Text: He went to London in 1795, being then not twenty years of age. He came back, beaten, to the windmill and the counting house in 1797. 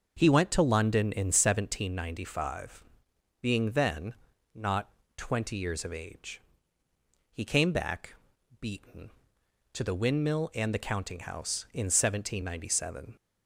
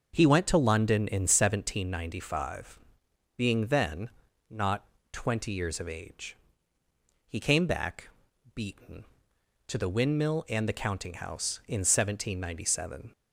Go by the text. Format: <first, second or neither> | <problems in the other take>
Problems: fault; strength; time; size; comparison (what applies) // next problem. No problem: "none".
neither | starts louder than the rest; noticeable; the same in both // pauses between "then" and "not"; slight; the same in both // pauses between "not" and "twenty"; slight; the same in both